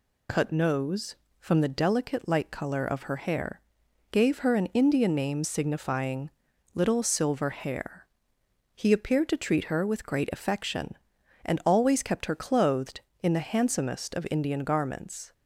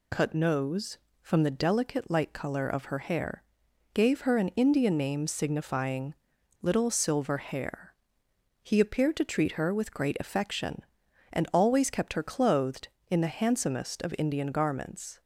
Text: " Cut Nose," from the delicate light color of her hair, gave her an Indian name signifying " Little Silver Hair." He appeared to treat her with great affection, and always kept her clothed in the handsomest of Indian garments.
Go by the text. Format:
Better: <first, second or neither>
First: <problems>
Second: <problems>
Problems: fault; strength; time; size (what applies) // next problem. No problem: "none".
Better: neither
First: none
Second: none